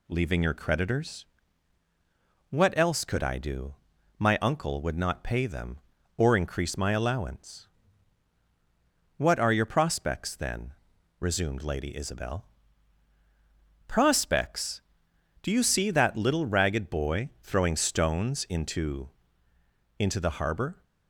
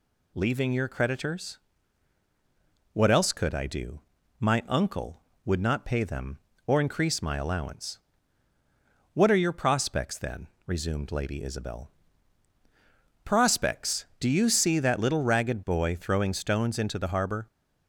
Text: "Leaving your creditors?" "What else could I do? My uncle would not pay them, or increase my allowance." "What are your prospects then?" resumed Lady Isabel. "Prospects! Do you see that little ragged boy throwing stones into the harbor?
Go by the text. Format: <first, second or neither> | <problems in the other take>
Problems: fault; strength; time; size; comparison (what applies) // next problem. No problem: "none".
second | says "into" twice; at 19.9 s